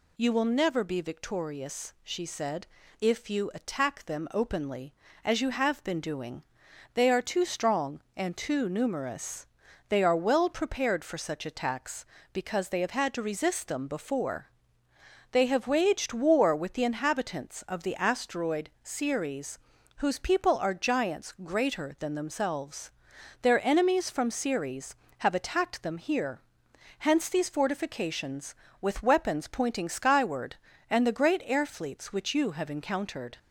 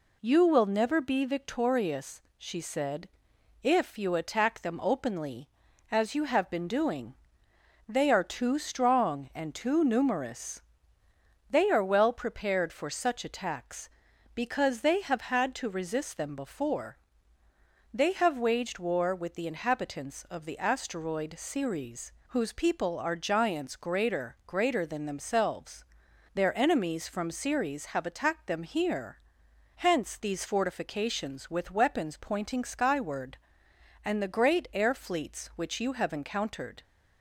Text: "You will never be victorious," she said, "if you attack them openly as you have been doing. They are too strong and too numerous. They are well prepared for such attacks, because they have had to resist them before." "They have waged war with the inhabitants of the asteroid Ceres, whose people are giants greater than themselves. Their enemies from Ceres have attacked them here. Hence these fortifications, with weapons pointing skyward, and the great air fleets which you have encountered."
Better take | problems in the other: first | says "greater" twice; at 24.4 s

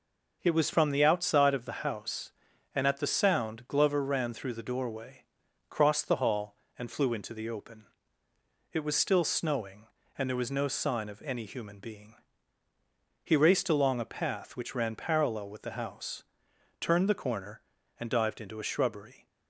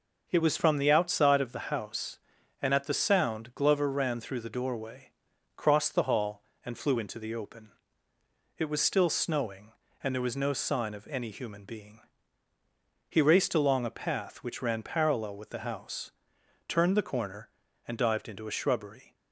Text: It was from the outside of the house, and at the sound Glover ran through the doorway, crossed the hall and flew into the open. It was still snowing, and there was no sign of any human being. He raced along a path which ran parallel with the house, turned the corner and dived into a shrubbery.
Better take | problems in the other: neither | none

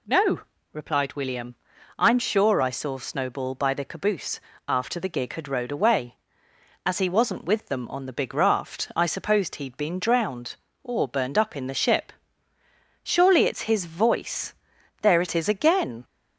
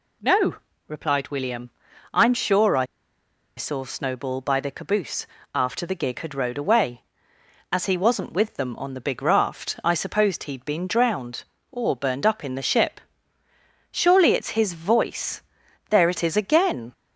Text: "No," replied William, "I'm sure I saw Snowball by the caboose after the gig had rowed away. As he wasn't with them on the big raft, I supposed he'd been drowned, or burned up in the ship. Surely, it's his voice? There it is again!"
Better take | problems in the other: first | pauses between "I" and "saw"; noticeable; at 2.8 s; 0.73 s long // pauses between "caboose" and "after"; slight; at 5.2 s; 0.30 s long; slight in the first

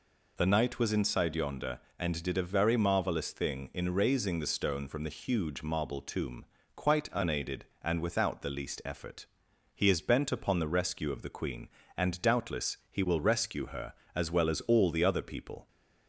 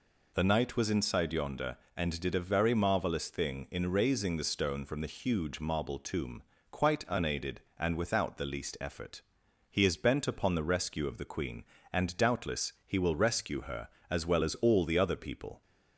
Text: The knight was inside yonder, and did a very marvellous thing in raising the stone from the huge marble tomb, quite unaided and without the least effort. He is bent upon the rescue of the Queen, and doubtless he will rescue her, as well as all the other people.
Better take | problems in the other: neither | none

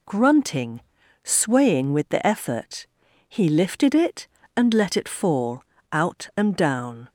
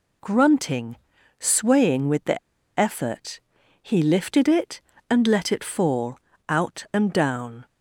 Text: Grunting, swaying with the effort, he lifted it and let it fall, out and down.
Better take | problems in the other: first | pauses between "the" and "effort"; at 2.3 s; 0.40 s long

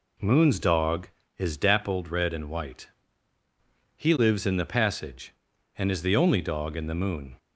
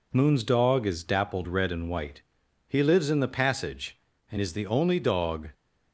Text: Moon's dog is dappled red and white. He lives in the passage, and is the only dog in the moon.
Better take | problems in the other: first | stops before "in the moon"; at 5.5 s

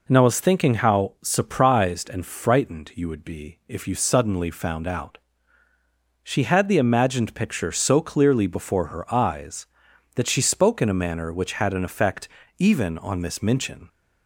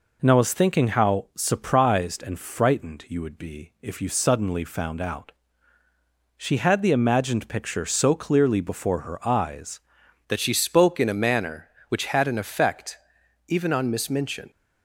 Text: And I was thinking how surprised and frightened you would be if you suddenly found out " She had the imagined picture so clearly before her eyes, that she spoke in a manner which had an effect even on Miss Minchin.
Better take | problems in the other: first | changes voice at "that"; from 10.2 s on; 4.3 s long // pauses between "effect" and "even"; noticeable; at 12.9 s; 0.52 s long; slight in the first

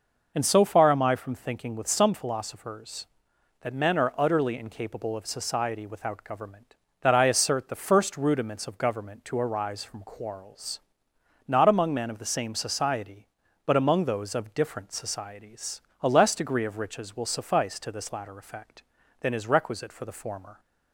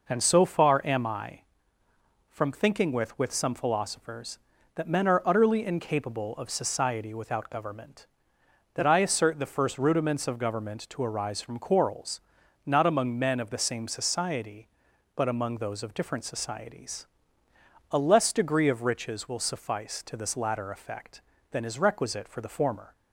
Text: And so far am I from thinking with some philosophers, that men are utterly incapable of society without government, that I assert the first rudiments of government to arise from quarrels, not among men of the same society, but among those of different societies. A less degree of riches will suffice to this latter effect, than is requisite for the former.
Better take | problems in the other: first | says "with" twice; at 3.1 s

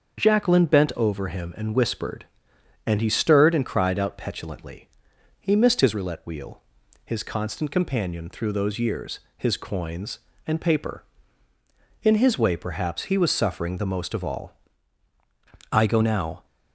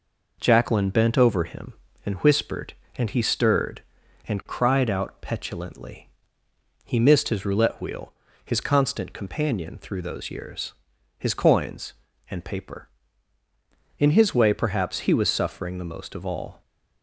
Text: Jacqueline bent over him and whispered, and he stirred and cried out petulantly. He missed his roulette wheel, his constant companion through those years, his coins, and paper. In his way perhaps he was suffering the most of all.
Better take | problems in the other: second | starts louder than the rest; until 1.2 s; 7 dB // goes on to say "I go now"; noticeable; from 15.7 s on; 0.74 s long

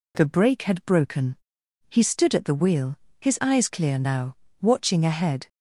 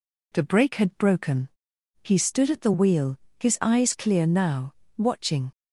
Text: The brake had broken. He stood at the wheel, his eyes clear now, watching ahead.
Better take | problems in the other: first | stops before "ahead"; at 5.5 s

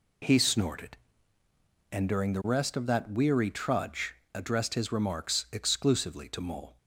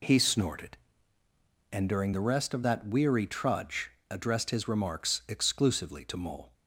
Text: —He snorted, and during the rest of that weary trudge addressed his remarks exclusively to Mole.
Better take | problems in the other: neither | pauses between "trudge" and "addressed"; slight; the same in both

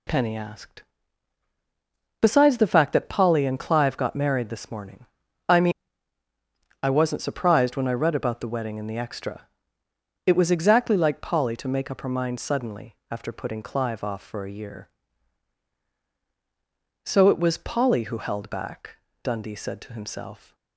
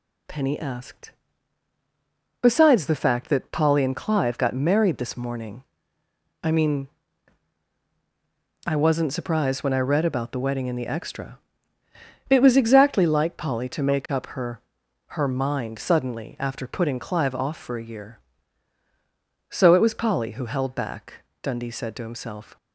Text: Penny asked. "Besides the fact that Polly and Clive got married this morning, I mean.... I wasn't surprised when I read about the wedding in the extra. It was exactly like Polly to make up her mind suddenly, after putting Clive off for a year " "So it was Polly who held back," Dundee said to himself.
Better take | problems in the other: first | says "her" twice; at 15.1 s

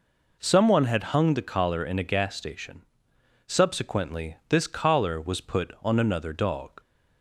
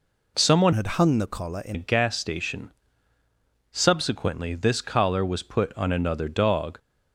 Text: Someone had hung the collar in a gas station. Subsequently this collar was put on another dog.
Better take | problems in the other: first | changes voice from "had" to "in"; from 0.7 to 1.7 s; 1.0 s long

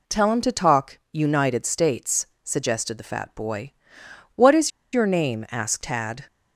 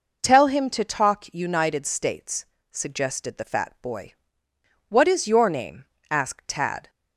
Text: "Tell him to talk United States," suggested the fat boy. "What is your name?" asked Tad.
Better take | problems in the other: second | pauses between "is" and "your"; slight; at 4.7 s; 0.23 s long

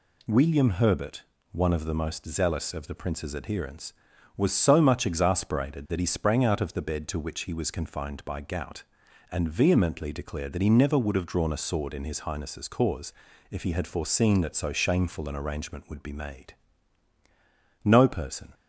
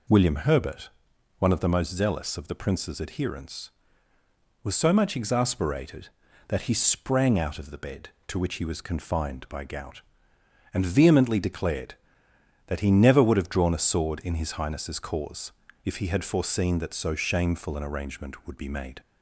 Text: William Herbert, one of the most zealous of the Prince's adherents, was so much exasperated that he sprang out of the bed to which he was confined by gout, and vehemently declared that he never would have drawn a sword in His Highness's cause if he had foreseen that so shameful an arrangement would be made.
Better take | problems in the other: second | pauses between "cause" and "if"; at 13.1 s; 0.38 s long; slight in the second // goes on to say "No person"; noticeable; from 17.8 s on; 0.70 s long

